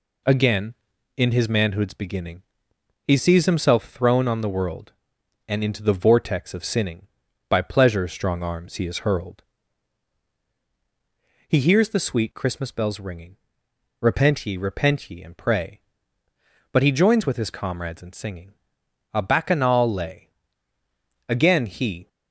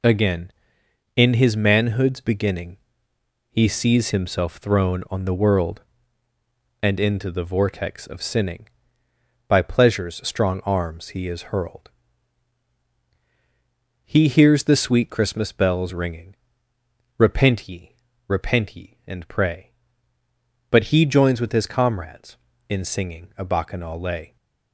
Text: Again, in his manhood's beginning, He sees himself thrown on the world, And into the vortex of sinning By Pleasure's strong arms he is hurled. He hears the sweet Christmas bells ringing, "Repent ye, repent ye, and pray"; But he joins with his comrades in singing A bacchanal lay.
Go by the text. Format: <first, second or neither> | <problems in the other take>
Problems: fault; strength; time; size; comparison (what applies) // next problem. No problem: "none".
second | pauses between "singing" and "A"; noticeable; at 18.5 s; 0.58 s long // goes on to say "Again he"; noticeable; from 21.2 s on; 0.80 s long